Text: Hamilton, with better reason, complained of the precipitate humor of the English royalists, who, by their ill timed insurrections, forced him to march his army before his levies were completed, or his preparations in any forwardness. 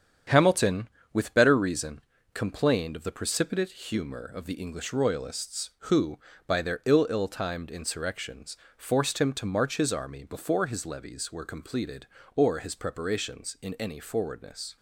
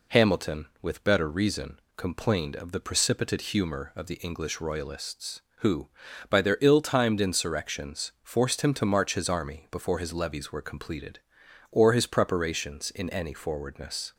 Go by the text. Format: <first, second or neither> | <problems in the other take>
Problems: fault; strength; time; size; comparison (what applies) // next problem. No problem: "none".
second | starts louder than the rest; strong; until 1.5 s; 8 dB // says "ill" twice; at 7.0 s